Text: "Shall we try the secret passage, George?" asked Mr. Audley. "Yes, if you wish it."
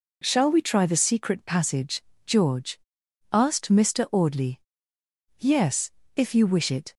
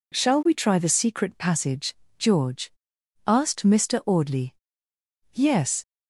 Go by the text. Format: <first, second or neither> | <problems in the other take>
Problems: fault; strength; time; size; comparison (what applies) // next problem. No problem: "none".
first | stops before "if you wish it"; at 5.8 s